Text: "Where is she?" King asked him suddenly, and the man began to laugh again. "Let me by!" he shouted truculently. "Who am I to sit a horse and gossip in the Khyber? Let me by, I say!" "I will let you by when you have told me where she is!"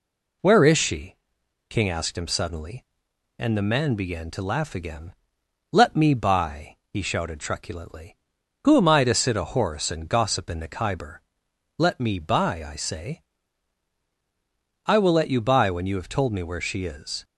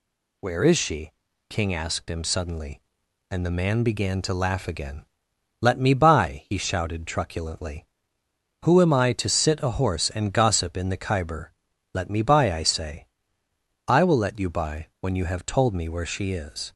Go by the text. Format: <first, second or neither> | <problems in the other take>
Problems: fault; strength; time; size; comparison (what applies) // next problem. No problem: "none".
neither | none